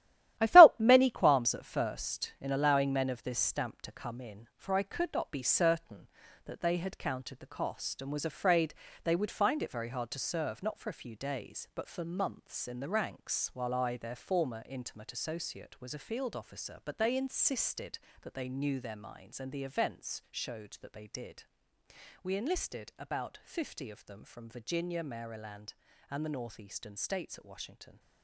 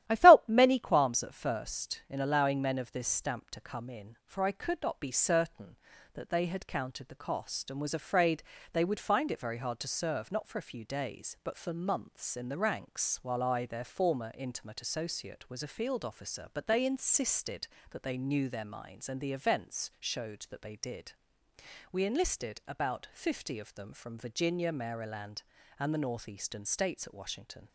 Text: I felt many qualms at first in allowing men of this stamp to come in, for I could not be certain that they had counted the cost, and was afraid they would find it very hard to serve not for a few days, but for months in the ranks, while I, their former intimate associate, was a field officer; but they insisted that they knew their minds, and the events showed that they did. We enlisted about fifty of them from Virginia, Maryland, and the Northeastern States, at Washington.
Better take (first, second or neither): second